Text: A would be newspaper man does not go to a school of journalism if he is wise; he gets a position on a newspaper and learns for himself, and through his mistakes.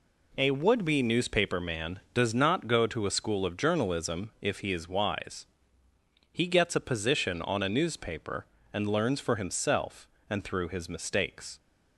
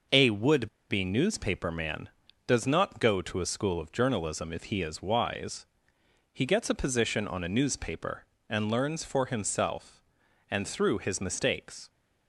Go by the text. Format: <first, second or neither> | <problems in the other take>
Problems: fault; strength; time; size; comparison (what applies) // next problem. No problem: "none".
first | pauses between "would" and "be"; slight; at 0.6 s; 0.21 s long